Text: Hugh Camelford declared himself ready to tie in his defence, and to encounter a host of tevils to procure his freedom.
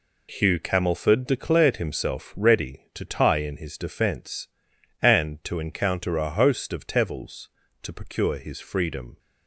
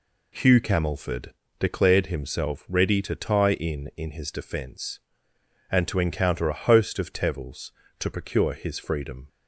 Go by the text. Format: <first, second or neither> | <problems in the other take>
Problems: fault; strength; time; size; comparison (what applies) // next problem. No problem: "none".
first | pauses between "Camelford" and "declared"; slight; at 1.3 s; 0.28 s long // says "in" twice; at 3.9 s